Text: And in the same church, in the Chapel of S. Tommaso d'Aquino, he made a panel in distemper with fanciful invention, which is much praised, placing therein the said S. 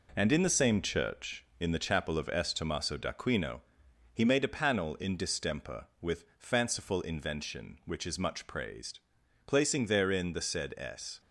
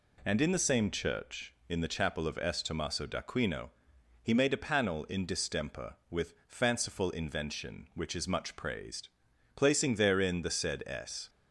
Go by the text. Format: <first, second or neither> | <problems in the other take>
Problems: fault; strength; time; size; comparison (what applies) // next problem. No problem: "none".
second | gets quieter; noticeable; throughout; 5.5 dB